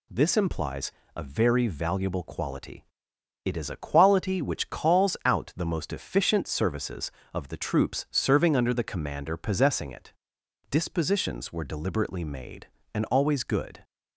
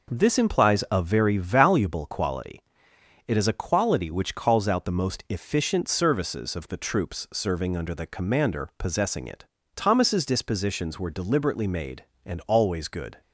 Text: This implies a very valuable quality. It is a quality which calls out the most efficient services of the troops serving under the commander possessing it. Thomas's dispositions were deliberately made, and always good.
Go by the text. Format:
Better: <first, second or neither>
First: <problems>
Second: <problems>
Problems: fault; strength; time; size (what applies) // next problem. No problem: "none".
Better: second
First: pauses between "implies" and "a"; slight; at 0.9 s; 0.24 s long // skips "Thomas's"; at 10.4 s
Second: none